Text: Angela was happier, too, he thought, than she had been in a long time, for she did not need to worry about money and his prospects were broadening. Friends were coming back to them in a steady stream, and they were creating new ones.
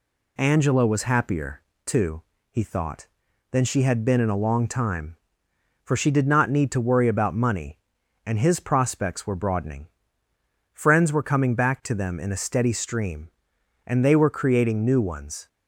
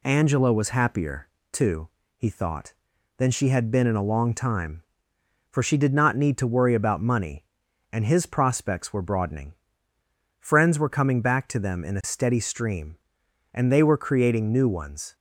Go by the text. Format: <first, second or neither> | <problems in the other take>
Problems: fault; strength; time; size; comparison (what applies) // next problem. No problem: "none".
neither | none